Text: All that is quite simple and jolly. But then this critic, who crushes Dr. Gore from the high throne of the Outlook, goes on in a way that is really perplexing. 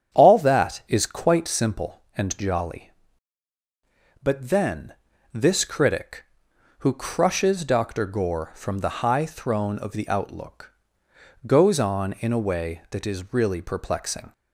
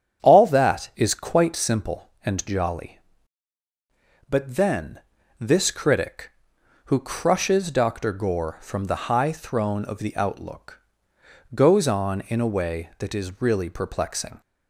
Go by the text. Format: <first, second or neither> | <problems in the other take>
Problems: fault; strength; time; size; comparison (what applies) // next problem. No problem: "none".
neither | starts louder than the rest; strong; the same in both // pauses between "then" and "this"; the same in both